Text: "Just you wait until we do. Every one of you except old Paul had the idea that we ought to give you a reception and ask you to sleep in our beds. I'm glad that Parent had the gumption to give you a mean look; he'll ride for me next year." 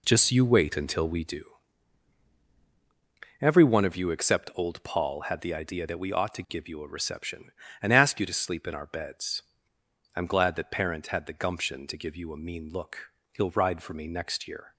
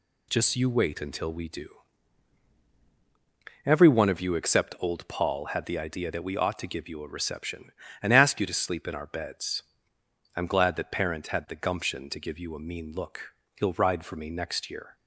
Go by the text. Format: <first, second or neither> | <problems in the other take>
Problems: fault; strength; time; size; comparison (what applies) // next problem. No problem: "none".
second | starts louder than the rest; slight; until 1.4 s; 3 dB